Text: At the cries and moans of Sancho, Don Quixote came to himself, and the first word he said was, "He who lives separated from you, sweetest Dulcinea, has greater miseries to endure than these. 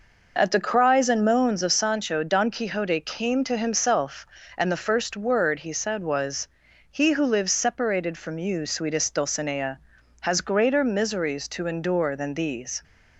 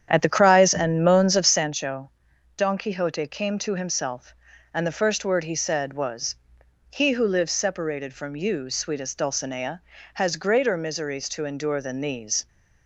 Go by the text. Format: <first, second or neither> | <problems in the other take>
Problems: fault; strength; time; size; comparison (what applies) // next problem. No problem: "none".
first | starts louder than the rest; strong; until 1.8 s; 9 dB